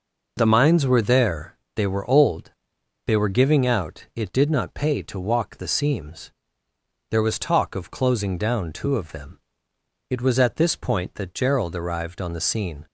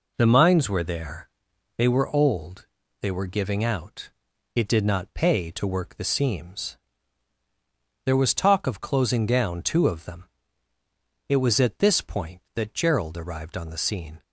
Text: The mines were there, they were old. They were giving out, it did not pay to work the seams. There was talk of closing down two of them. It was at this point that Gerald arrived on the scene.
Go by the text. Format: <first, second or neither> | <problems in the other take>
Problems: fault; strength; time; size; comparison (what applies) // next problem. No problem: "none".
second | says "walk" for "work"; at 5.1 s